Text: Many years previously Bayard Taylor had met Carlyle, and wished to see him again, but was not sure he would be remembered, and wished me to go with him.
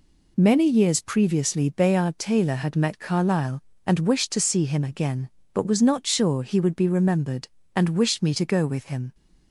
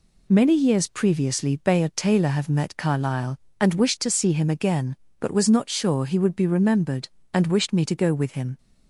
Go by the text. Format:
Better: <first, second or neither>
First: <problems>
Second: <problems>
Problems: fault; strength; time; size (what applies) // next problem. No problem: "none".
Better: first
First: none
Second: says "have" for "had"; at 2.2 s